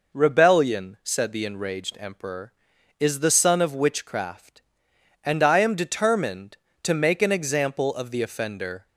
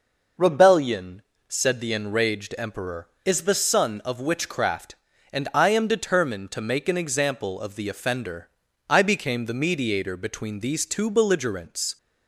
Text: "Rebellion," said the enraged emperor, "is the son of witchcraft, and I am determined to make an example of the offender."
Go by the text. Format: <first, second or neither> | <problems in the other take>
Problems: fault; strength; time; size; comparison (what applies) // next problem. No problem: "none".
first | goes on to say "I became the mediator between these two belligerents"; strong; from 8.8 s on; 3.0 s long